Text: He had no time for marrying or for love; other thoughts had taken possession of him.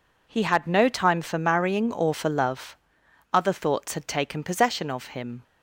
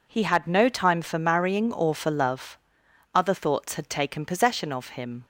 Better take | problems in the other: neither | none

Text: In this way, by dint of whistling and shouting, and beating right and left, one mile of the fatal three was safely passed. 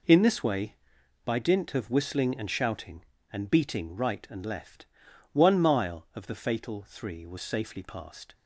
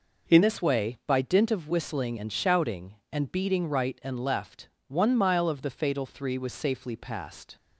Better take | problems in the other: first | changes voice at "this"; from 0.4 s on; 7.1 s long

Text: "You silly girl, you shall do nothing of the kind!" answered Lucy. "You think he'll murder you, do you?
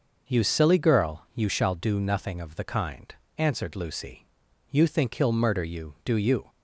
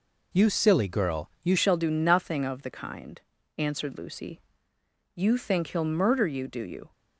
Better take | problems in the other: first | changes voice at "shall"; from 1.5 s on; 5.4 s long

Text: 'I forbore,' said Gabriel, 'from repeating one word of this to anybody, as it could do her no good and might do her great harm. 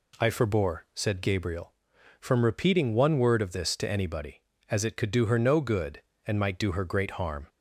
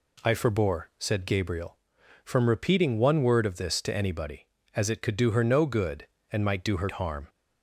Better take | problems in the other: first | skips "great"; at 6.9 s

